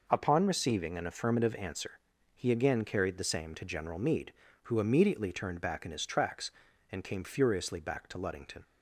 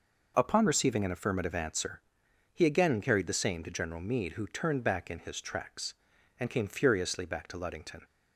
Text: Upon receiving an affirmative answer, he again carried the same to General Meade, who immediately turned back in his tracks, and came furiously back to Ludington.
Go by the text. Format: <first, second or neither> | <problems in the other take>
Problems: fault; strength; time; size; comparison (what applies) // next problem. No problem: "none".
first | skips "immediately"; at 4.4 s